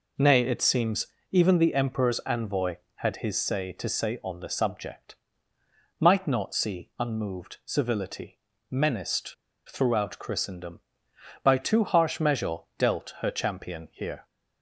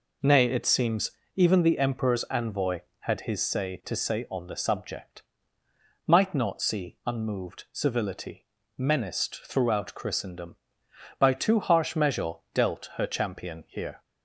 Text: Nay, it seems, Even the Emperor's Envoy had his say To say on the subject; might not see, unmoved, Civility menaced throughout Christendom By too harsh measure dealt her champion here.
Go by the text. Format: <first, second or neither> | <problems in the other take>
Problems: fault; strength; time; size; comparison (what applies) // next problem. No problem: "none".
second | pauses between "Civility" and "menaced"; slight; at 8.3 s; 0.32 s long; slight in the second // pauses between "menaced" and "throughout"; slight; at 9.3 s; 0.34 s long // pauses between "measure" and "dealt"; slight; at 12.5 s; 0.18 s long; slight in the second